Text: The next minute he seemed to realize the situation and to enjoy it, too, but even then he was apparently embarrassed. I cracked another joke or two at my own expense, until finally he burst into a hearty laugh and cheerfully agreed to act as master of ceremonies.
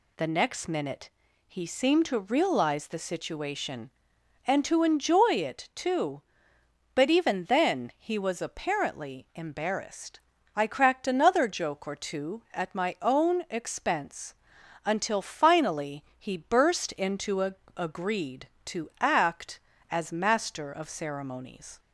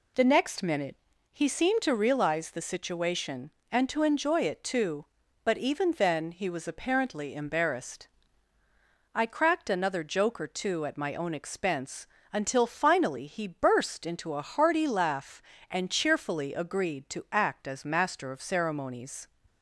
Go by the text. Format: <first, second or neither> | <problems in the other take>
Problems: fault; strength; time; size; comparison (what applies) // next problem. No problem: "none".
second | pauses between "minute" and "he"; at 1.0 s; 0.38 s long; slight in the second // pauses between "finally" and "he"; slight; at 16.0 s; 0.16 s long // skips "hearty laugh and cheerfully"; at 17.6 s